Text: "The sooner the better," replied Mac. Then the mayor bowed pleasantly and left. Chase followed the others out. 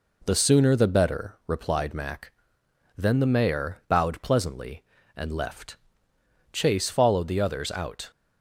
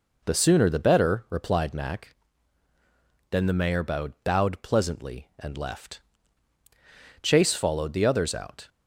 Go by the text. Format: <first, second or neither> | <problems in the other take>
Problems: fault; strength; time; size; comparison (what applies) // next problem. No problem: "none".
first | says "bowed" twice; at 4.2 s